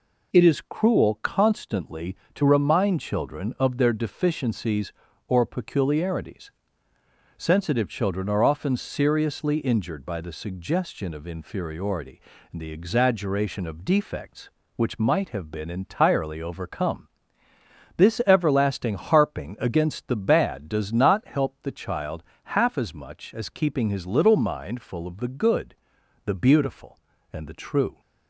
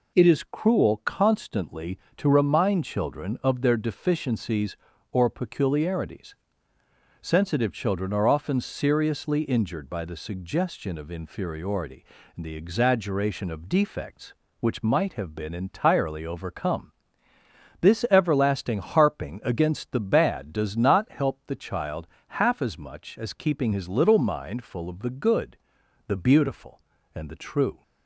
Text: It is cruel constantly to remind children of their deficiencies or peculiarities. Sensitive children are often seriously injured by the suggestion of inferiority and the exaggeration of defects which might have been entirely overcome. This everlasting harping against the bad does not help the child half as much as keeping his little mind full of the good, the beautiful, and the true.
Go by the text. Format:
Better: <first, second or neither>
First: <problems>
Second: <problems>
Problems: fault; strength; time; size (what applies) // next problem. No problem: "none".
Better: neither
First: pauses between "child" and "half"; slight; at 22.2 s; 0.22 s long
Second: pauses between "child" and "half"; slight; at 22.0 s; 0.22 s long